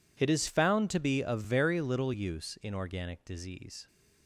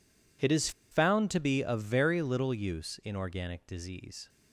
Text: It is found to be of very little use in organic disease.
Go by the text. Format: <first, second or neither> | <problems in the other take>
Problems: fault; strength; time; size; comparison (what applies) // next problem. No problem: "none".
first | pauses between "is" and "found"; slight; at 0.6 s; 0.21 s long